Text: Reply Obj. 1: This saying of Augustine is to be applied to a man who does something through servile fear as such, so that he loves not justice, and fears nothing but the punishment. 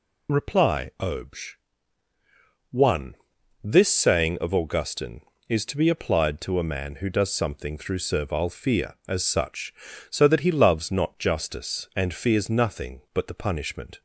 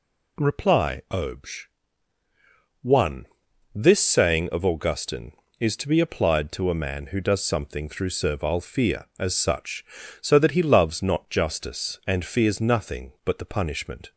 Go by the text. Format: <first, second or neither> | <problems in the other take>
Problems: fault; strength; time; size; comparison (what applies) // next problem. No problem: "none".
second | loses the start of "Reply"; at 0.2 s; 25 ms